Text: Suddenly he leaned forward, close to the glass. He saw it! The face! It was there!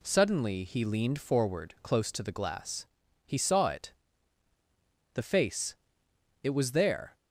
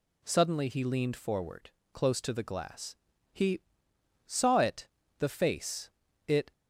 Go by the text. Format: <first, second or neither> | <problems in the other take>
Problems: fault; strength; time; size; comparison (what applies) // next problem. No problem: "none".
first | pauses between "He" and "saw"; noticeable; at 3.6 s; 0.66 s long // stops before "was there"; at 6.5 s